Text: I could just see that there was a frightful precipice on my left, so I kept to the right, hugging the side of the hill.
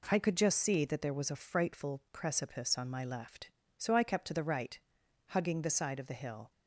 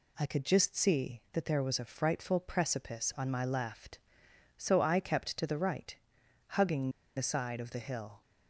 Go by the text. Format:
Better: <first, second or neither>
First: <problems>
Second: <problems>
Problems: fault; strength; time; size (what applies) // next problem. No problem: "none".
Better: first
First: none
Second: pauses between "hugging" and "the"; slight; at 6.9 s; 0.25 s long